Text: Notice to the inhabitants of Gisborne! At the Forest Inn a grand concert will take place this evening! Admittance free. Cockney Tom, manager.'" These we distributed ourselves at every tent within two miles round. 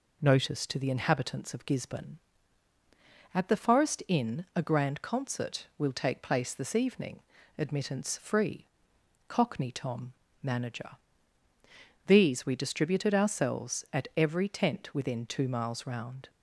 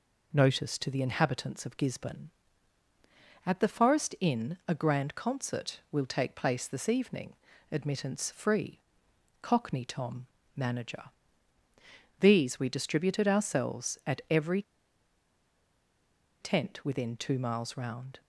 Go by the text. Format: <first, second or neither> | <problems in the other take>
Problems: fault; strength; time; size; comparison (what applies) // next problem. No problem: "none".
first | pauses between "every" and "tent"; strong; at 14.6 s; 1.7 s long